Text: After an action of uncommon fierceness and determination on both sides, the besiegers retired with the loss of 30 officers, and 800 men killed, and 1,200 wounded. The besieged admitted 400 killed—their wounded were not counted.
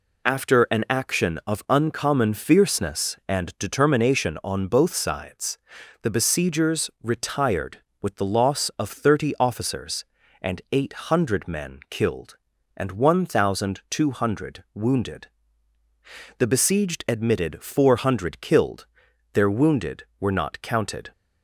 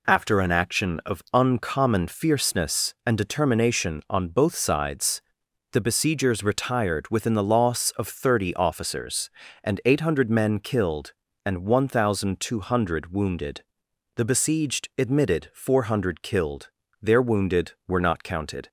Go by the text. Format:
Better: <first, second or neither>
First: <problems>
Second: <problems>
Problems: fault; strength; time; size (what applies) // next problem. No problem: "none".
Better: first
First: none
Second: says "within" for "with"; at 7.0 s